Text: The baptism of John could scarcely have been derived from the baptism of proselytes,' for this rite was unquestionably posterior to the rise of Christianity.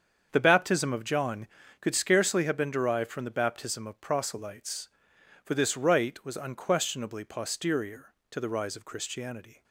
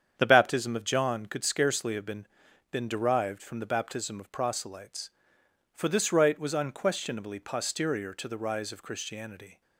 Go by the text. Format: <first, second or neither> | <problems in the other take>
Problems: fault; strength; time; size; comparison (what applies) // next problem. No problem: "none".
first | starts louder than the rest; strong; until 1.1 s; 8 dB; strong in the first // says "been" twice; at 2.7 s